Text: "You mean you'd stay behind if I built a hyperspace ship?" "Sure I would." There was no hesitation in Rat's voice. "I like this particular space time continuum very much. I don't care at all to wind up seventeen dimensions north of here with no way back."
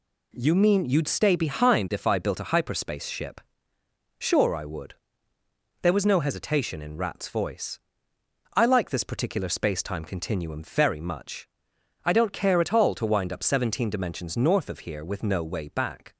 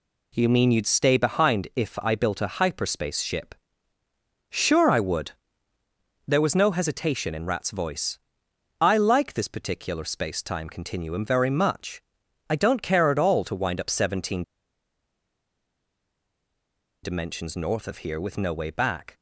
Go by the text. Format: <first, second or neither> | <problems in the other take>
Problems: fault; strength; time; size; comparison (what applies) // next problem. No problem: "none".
first | pauses between "seventeen" and "dimensions"; strong; at 14.4 s; 2.6 s long